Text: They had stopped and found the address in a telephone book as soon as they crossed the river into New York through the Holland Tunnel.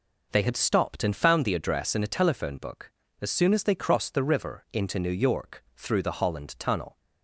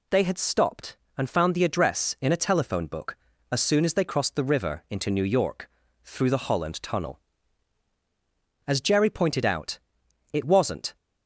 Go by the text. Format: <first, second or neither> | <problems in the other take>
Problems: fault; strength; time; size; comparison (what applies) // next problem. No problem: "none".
first | pauses between "York" and "through"; slight; at 5.6 s; 0.36 s long // goes on to say "As Jerry pointed out it wasn't"; strong; from 8.6 s on; 2.3 s long